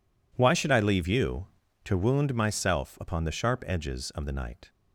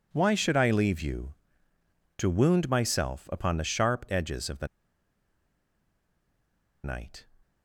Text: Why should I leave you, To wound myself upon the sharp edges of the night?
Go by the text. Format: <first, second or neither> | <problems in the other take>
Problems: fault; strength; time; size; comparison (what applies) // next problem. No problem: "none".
first | pauses between "the" and "night"; strong; at 4.6 s; 2.1 s long